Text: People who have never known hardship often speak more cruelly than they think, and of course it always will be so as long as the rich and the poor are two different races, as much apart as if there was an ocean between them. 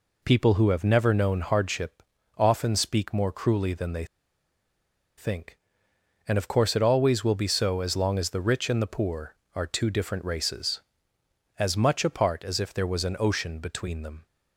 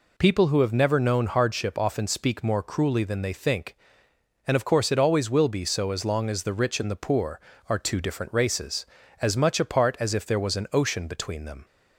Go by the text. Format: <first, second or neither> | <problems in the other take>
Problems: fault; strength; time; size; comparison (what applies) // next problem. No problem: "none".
second | pauses between "hardship" and "often"; slight; at 2.0 s; 0.36 s long // pauses between "they" and "think"; at 4.0 s; 1.1 s long